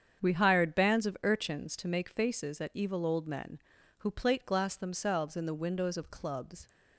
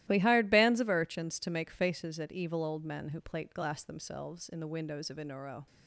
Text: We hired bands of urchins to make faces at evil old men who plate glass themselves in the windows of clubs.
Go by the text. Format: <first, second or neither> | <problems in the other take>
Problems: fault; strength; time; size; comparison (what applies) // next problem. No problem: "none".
first | starts louder than the rest; strong; until 1.0 s; 15 dB; strong in the first // says "inuro" for "clubs"; at 5.1 s